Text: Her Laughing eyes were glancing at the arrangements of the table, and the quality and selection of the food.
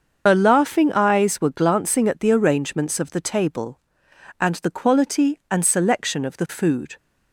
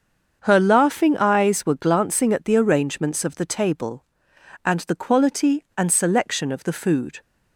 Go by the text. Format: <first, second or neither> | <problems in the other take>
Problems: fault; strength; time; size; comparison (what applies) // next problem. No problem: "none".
second | loses the start of "Her"; at 0.2 s; 90 ms // starts louder than the rest; until 1.2 s; 6.5 dB; also in the second